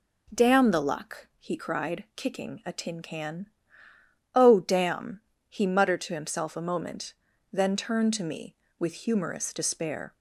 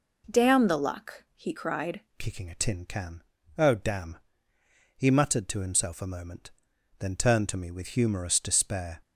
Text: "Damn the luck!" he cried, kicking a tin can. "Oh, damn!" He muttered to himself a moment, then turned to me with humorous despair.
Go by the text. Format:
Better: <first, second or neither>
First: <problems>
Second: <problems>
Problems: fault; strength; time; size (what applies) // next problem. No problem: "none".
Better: first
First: none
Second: changes voice at "kicking"; from 2.1 s on; 6.9 s long